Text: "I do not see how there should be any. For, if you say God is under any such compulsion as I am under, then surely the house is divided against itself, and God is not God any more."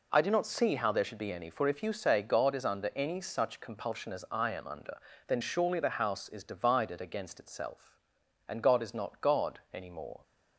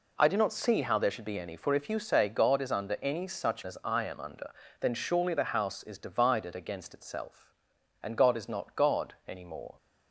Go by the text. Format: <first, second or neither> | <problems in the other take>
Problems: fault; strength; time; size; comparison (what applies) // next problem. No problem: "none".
first | skips "compulsion"; at 3.6 s